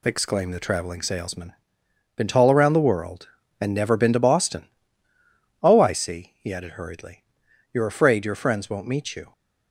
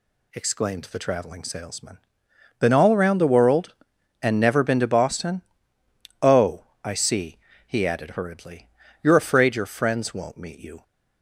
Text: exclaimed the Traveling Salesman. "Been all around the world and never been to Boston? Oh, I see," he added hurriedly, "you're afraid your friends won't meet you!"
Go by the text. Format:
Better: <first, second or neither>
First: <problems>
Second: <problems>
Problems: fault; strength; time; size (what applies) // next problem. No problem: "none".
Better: second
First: says "tall" for "all"; at 2.2 s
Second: none